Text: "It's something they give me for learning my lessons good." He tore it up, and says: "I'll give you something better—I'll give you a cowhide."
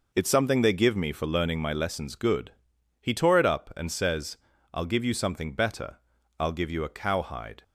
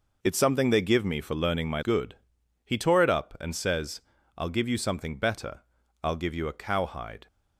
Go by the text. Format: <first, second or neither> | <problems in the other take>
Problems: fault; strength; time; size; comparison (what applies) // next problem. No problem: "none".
first | skips "lessons"; at 1.8 s